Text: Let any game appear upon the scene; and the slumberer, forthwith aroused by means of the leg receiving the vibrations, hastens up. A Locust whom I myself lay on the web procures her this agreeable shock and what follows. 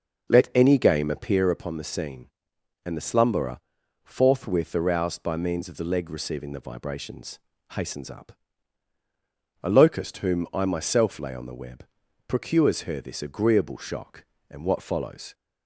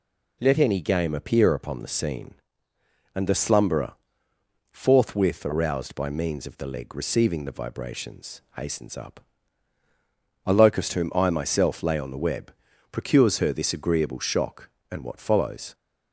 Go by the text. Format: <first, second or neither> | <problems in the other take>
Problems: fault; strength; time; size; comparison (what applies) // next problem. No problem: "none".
second | starts louder than the rest; noticeable; until 1.4 s; 5.5 dB // pauses between "web" and "procures"; at 11.8 s; 0.42 s long; also in the second